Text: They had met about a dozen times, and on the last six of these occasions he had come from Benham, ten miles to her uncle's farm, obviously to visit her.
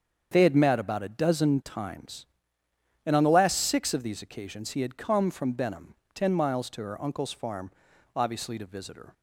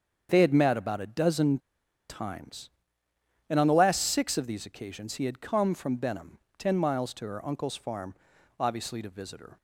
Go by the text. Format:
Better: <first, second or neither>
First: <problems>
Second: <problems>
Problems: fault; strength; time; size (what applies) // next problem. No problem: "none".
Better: first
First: starts louder than the rest; strong; until 1.3 s; 7.5 dB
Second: starts louder than the rest; strong; until 1.3 s; 7.5 dB // pauses between "dozen" and "times"; noticeable; at 1.5 s; 0.51 s long